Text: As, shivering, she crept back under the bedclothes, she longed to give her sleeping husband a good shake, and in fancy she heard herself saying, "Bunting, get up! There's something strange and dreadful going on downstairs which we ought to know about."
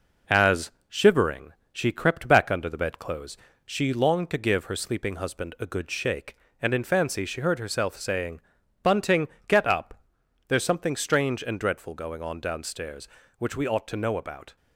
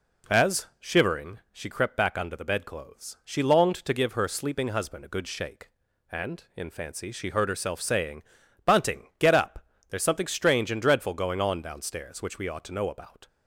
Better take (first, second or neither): second